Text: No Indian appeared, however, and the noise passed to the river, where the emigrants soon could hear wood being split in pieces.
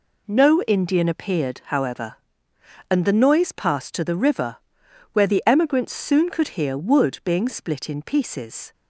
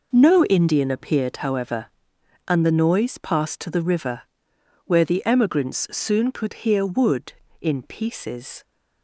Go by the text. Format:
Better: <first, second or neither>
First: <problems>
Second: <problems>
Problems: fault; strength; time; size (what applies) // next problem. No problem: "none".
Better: first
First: none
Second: skips "being split"; at 7.4 s